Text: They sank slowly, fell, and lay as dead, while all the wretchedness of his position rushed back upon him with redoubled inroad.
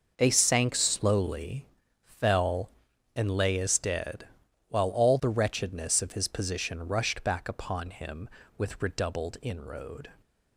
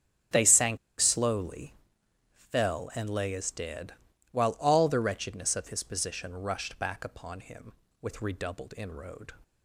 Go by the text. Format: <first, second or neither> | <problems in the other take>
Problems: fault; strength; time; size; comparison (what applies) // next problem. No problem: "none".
first | starts louder than the rest; strong; until 1.5 s; 8 dB // pauses between "sank" and "slowly"; slight; at 0.7 s; 0.22 s long